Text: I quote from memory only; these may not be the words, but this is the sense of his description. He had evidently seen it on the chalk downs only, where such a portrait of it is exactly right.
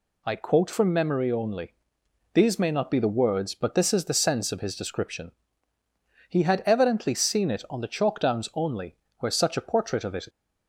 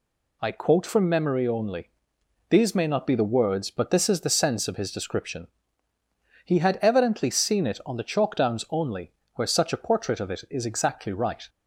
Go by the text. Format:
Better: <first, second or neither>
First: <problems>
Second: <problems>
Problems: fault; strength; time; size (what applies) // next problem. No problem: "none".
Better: second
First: stops before "is exactly right"; at 10.2 s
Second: none